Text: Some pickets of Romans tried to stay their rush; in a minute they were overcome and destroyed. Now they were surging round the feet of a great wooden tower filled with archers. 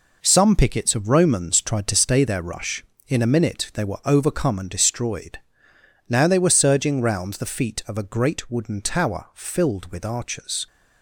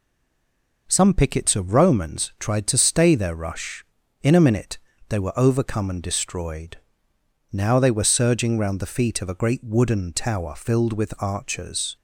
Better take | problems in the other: first | stays silent before the first word; slight; until 0.8 s; 0.8 s long // pauses between "minute" and "they"; slight; at 4.7 s; 0.30 s long

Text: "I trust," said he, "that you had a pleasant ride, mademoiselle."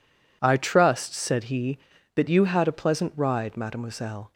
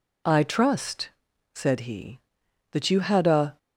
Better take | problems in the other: first | stops before "pleasant ride mademoiselle"; at 3.5 s

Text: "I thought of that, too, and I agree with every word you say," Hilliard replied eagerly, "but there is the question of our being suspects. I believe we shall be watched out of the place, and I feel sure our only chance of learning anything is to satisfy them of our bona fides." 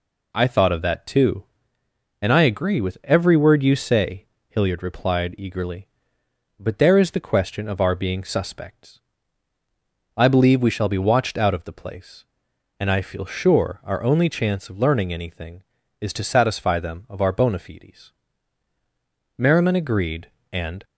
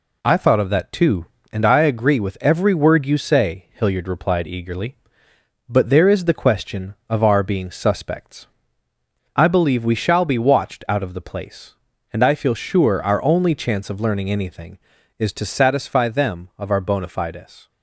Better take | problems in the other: second | goes on to say "Merriman agreed and"; from 19.3 s on; 1.4 s long

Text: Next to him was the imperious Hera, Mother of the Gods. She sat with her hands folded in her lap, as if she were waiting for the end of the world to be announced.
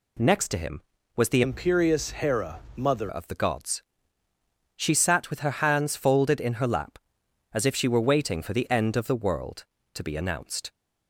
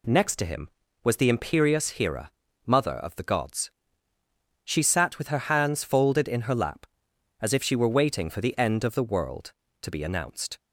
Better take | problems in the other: second | changes voice from "imperious" to "Mother"; from 1.4 to 3.1 s; 1.7 s long

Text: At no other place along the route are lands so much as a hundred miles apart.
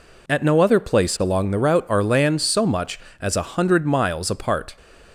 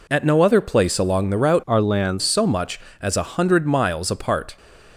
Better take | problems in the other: first | changes voice from "are" to "lands"; from 1.6 to 2.2 s; 0.6 s long

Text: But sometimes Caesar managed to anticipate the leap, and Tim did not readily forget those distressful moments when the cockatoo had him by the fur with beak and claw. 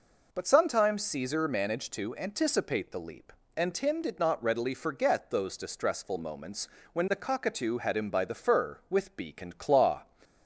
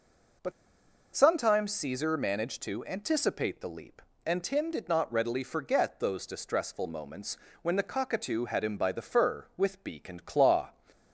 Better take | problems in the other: first | pauses between "But" and "sometimes"; noticeable; at 0.5 s; 0.63 s long // pauses between "moments" and "when"; slight; at 7.3 s; 0.24 s long; slight in the first

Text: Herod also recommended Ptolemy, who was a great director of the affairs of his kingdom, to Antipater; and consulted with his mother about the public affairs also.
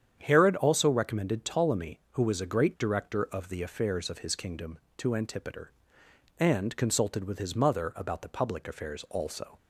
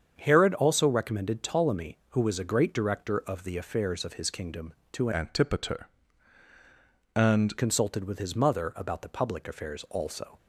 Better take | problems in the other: first | starts louder than the rest; strong; until 1.1 s; 7.5 dB; strong in the first // changes voice from "Antipater" to "and"; from 5.1 to 7.5 s; 2.4 s long

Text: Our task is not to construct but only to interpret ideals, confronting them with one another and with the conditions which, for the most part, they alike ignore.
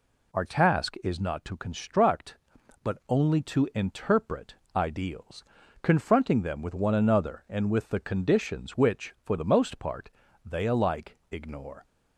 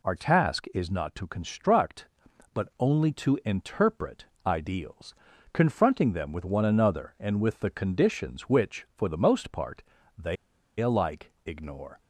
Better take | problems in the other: first | pauses between "interpret" and "ideals"; slight; at 4.2 s; 0.20 s long; slight in the first // pauses between "they" and "alike"; at 10.3 s; 0.44 s long

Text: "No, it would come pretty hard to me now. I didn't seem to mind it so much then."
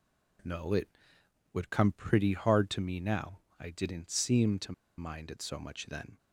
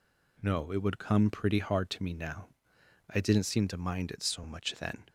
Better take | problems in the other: second | pauses between "to" and "mind"; slight; at 4.7 s; 0.25 s long

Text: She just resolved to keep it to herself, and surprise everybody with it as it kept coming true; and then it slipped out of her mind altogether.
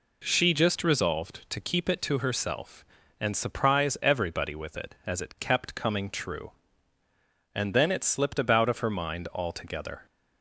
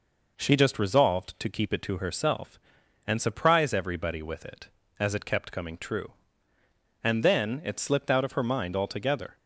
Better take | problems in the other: second | says "about" for "out"; at 8.3 s

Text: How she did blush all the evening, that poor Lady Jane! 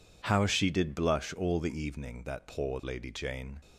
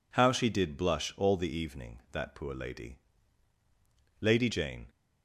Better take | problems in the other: first | says "Lady" twice; at 4.1 s

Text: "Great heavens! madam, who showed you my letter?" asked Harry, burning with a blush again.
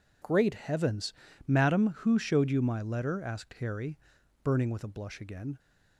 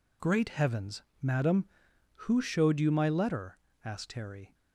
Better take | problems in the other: first | stops before "burning with a blush again"; at 4.5 s

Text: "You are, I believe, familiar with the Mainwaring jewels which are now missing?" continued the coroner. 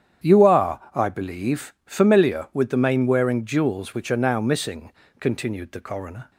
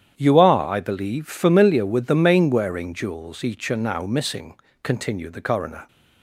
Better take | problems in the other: first | starts louder than the rest; strong; until 1.2 s; 9 dB; strong in the first // says "each" for "which"; at 3.4 s

